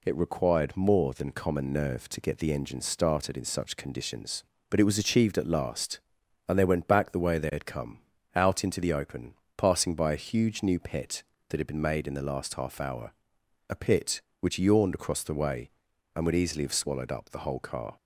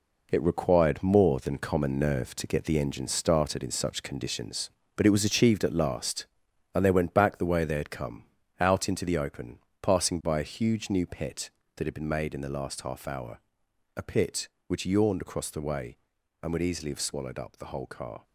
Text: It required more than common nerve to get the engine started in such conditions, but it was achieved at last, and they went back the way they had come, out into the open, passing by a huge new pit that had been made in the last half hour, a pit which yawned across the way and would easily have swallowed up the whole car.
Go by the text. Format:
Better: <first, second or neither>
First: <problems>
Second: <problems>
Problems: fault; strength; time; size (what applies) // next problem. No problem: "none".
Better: first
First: none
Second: gets quieter; strong; throughout; 8.5 dB